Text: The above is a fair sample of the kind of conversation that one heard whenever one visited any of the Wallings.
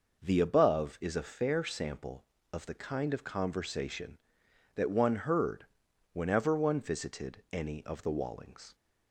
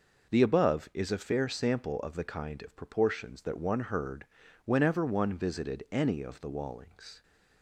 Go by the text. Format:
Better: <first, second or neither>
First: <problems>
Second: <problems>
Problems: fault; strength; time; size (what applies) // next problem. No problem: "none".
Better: first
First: pauses between "heard" and "whenever"; noticeable; at 5.6 s; 0.48 s long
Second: says "proportions" for "conversation"; at 2.7 s // pauses between "heard" and "whenever"; at 4.2 s; 0.40 s long